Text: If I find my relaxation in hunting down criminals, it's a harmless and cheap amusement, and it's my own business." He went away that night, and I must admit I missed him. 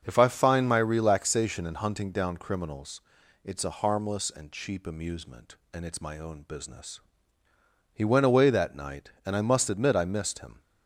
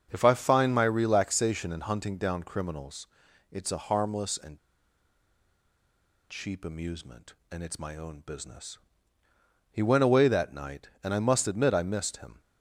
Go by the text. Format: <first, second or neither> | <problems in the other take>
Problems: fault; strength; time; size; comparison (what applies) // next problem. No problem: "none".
first | starts louder than the rest; until 1.1 s; 6.5 dB; also in the first // pauses between "and" and "cheap"; strong; at 4.5 s; 1.7 s long